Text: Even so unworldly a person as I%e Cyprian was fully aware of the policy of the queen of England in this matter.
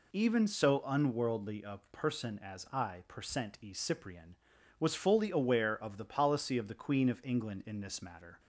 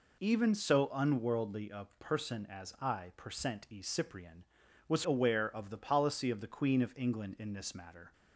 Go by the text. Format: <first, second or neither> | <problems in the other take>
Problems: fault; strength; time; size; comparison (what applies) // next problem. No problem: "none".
first | skips "fully"; at 5.0 s